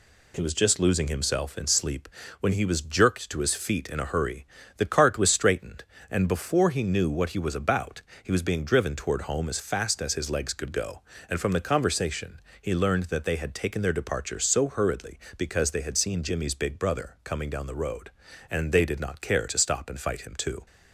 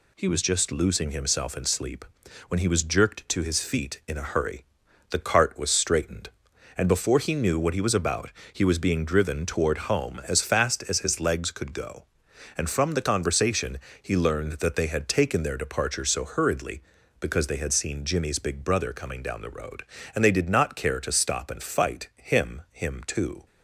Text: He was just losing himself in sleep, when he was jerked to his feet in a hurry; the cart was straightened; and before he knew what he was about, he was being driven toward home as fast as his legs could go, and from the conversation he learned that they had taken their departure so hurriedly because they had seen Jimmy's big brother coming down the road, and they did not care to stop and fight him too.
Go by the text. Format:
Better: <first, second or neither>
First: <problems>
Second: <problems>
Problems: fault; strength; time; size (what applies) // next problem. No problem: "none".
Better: first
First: pauses between "conversation" and "he"; slight; at 12.4 s; 0.18 s long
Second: pauses between "conversation" and "he"; slight; at 13.7 s; 0.24 s long // says "him" twice; at 22.7 s